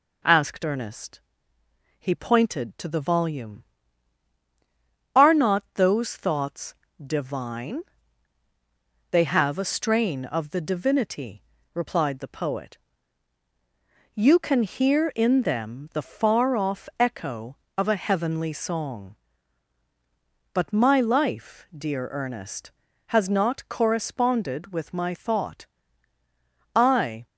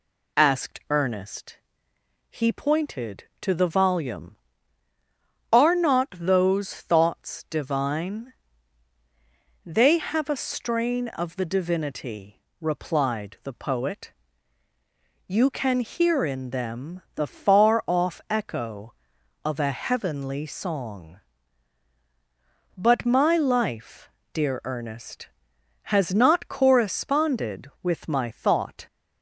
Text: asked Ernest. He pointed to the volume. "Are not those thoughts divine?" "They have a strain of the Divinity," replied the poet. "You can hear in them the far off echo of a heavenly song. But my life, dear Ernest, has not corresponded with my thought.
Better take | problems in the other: second | pauses between "thoughts" and "divine"; slight; at 6.7 s; 0.30 s long // goes on to say "I"; from 26.7 s on; 0.50 s long

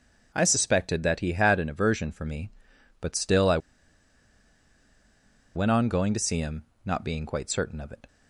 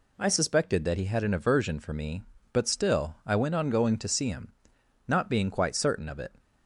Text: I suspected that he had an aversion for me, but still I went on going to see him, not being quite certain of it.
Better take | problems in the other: second | starts louder than the rest; until 1.3 s; 7 dB // pauses between "I" and "went"; strong; at 3.5 s; 1.9 s long

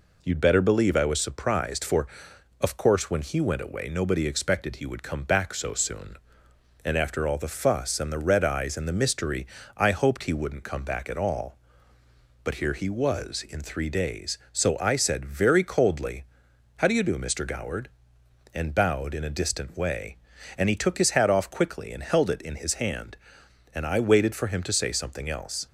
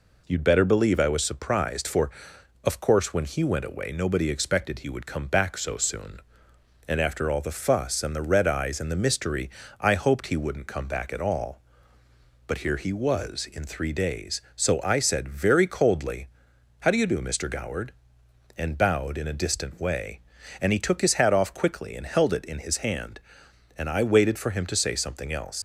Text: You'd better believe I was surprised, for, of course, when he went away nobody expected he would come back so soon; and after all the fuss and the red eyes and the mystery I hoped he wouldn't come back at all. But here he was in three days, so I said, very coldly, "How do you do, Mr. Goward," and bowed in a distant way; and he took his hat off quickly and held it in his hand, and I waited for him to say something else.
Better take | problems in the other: first | pauses between "mystery" and "I"; slight; at 9.4 s; 0.32 s long; slight in the first // leaves "else" unfinished; at 25.5 s; 75 ms

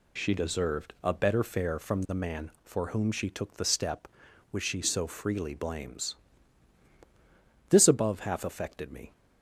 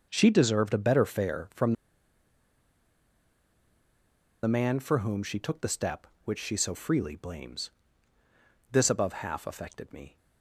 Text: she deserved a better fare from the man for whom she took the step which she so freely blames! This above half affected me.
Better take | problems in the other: first | starts louder than the rest; noticeable; until 1.1 s; 6 dB // pauses between "from" and "the"; strong; at 1.7 s; 2.7 s long

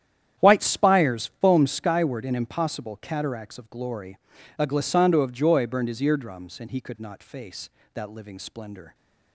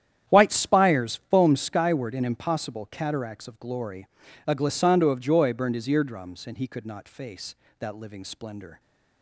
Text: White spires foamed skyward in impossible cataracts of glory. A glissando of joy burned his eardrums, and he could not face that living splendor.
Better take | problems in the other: neither | starts louder than the rest; strong; the same in both

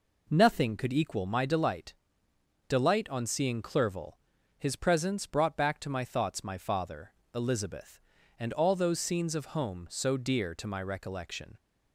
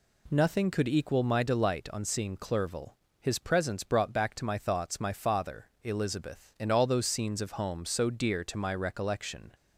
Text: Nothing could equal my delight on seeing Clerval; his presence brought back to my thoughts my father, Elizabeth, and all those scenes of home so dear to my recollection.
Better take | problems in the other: second | says "delight" twice; at 2.6 s

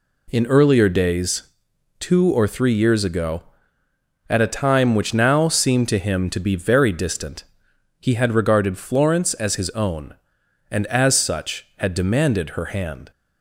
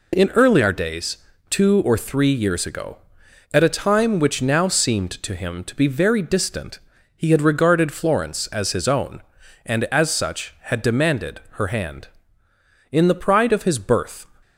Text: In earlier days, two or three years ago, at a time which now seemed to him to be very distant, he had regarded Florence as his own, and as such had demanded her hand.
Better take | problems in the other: first | goes on to say "In the pride of his birth"; from 12.9 s on; 1.3 s long

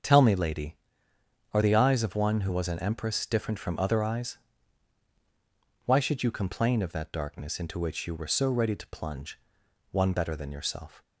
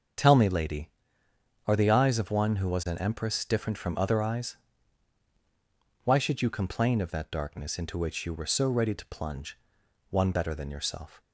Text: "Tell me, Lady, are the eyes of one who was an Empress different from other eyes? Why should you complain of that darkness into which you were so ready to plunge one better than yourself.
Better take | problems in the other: neither | starts louder than the rest; the same in both // pauses between "plunge" and "one"; noticeable; the same in both

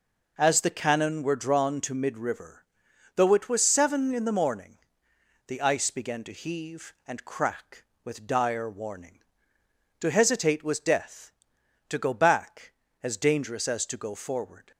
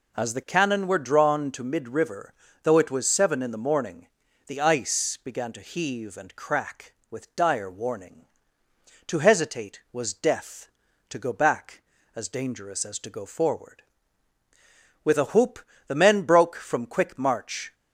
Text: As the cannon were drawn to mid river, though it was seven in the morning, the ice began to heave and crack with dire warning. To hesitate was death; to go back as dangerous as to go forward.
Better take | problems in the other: first | goes on to say "With a whoop the men broke from quick march"; strong; from 15.0 s on; 2.7 s long

